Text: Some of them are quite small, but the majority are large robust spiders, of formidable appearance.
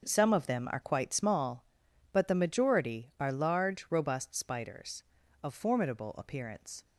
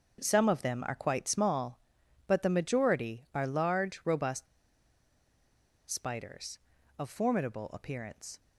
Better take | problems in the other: first | starts louder than the rest; until 1.2 s; 6 dB; also in the first // pauses between "robust" and "spiders"; strong; at 4.4 s; 1.4 s long

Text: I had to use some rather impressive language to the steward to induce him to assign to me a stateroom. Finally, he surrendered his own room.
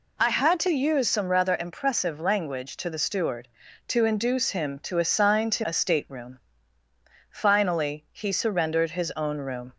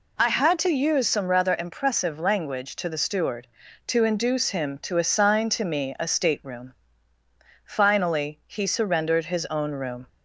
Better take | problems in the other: second | skips "me"; at 5.6 s

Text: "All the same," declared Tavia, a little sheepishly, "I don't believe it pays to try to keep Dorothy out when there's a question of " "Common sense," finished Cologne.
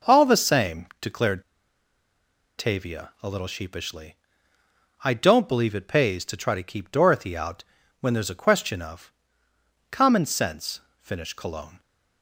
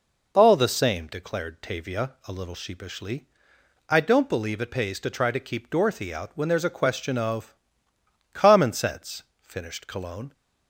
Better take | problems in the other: second | pauses between "declared" and "Tavia"; at 1.4 s; 1.1 s long // pauses between "out" and "when"; slight; at 7.6 s; 0.36 s long

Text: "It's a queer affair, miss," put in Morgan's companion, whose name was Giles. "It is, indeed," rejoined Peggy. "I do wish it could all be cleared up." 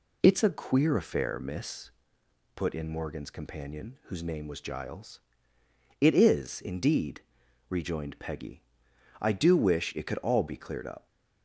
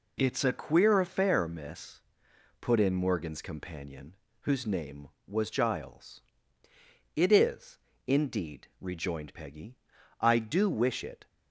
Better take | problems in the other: first | stops before "could all be cleared up"; at 11.2 s

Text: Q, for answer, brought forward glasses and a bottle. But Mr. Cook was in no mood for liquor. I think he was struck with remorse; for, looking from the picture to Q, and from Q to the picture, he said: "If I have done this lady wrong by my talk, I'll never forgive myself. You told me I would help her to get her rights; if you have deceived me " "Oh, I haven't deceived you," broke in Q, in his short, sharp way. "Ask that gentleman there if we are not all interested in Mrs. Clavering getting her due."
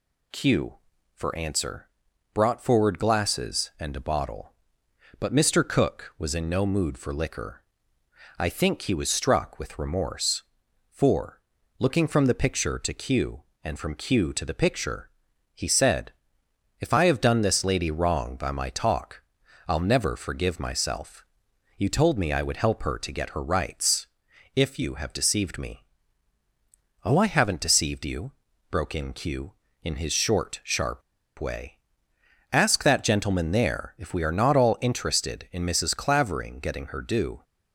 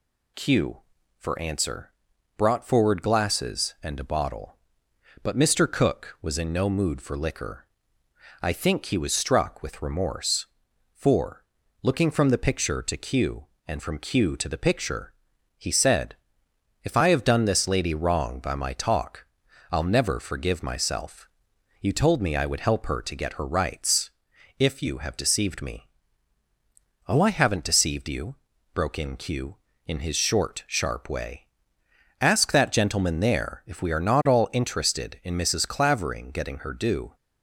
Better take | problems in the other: second | pauses between "sharp" and "way"; at 31.0 s; 0.37 s long

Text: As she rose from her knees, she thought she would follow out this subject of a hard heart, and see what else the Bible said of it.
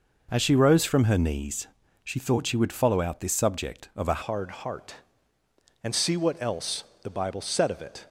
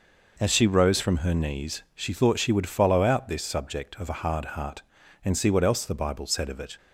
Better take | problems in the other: second | changes voice at "hard"; from 4.2 s on; 3.8 s long // pauses between "else" and "the"; slight; at 6.8 s; 0.18 s long

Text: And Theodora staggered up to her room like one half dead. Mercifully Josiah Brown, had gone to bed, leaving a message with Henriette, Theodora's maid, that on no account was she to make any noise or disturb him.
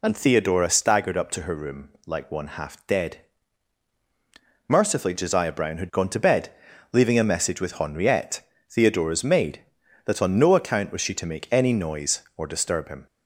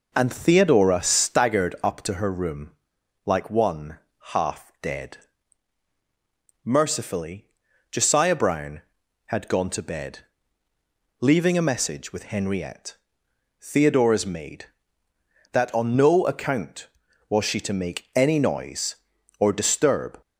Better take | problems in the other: first | pauses between "room" and "like"; noticeable; at 2.7 s; 0.52 s long; slight in the first // pauses between "one" and "half"; slight; at 3.9 s; 0.34 s long // pauses between "Mercifully" and "Josiah"; at 7.4 s; 0.44 s long // stops before "him"; at 20.2 s

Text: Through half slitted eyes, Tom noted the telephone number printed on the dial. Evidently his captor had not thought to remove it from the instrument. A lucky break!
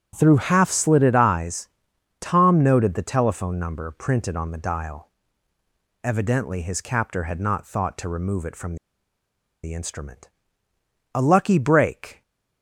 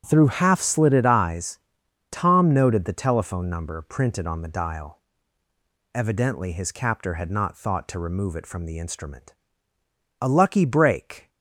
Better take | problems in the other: second | starts louder than the rest; strong; until 1.1 s; 8 dB; strong in the second // pauses between "from" and "the"; noticeable; at 8.7 s; 0.87 s long

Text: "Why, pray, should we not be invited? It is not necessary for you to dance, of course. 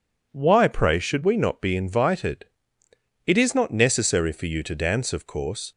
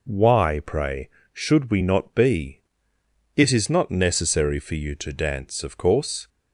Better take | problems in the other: first | skips "invited"; at 2.9 s

